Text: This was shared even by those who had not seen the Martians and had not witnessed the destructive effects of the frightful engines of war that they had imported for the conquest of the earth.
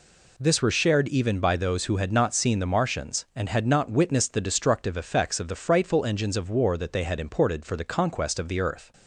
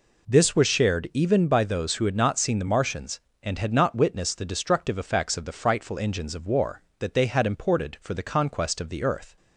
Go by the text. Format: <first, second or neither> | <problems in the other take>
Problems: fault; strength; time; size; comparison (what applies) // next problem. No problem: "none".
second | says "were" for "was"; at 0.6 s